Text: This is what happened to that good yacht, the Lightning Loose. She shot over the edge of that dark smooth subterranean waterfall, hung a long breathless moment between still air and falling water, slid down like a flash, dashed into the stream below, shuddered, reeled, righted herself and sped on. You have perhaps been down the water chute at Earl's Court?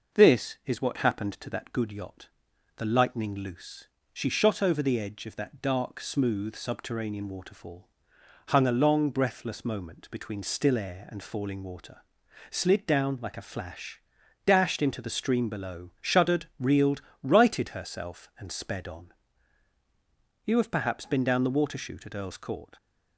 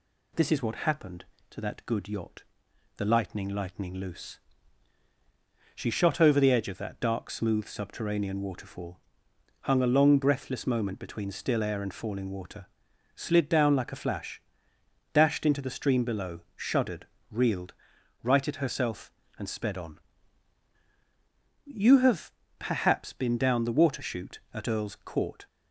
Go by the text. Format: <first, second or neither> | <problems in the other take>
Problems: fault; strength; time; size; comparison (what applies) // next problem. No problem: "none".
first | says "Lightning" twice; at 3.4 s // pauses between "have" and "perhaps"; slight; at 22.3 s; 0.26 s long